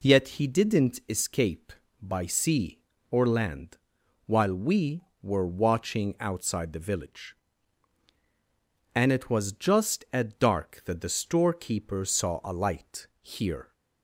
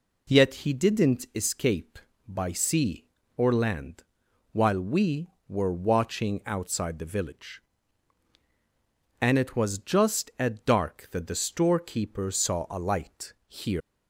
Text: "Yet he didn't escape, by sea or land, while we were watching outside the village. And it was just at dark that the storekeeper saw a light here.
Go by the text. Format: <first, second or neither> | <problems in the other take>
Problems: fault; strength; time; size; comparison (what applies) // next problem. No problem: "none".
first | pauses between "light" and "here"; slight; at 13.3 s; 0.16 s long; slight in the first // leaves "here" unfinished; at 13.8 s; 180 ms